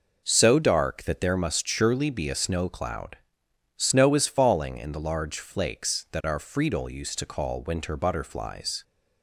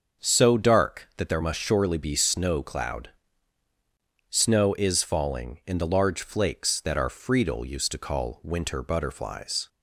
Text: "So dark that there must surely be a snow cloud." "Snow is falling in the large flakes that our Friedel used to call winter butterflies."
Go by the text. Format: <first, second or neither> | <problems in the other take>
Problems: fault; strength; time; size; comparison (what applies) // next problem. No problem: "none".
first | starts louder than the rest; until 1.2 s; 6.5 dB // skips "a"; at 2.1 s